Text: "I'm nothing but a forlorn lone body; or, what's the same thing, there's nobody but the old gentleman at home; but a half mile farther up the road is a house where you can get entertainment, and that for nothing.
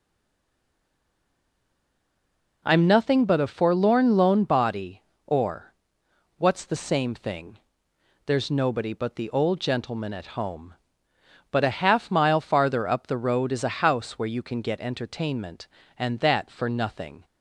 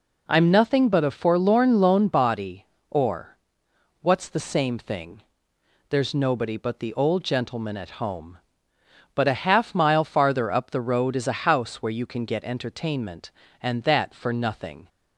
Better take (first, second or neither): second